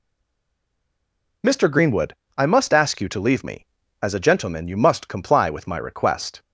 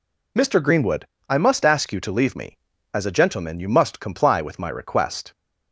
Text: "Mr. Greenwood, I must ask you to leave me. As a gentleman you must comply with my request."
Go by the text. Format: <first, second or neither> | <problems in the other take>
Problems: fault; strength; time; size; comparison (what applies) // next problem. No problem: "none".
second | stays silent before the first word; noticeable; until 1.4 s; 1.4 s long